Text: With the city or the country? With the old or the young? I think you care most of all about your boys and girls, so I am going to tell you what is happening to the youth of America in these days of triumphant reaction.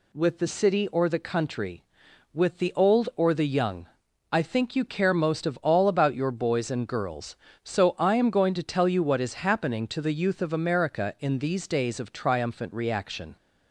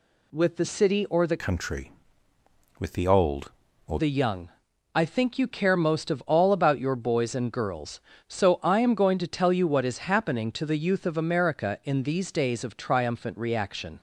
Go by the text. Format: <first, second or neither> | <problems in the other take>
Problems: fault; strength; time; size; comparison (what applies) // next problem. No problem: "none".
first | changes voice from "country" to "or"; from 1.4 to 4.0 s; 2.6 s long